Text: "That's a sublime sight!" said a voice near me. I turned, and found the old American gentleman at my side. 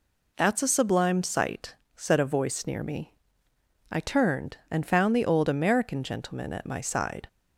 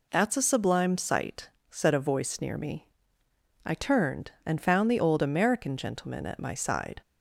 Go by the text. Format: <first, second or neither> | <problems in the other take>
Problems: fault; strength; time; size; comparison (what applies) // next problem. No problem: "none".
neither | none